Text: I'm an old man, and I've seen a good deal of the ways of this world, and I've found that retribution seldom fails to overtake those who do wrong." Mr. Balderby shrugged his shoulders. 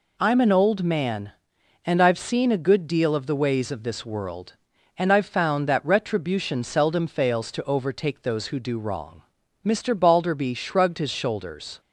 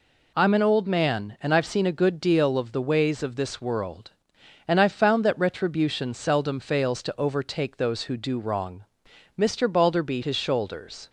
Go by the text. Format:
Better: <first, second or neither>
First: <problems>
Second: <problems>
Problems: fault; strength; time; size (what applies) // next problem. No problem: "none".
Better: first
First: none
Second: skips "shrugged"; at 10.2 s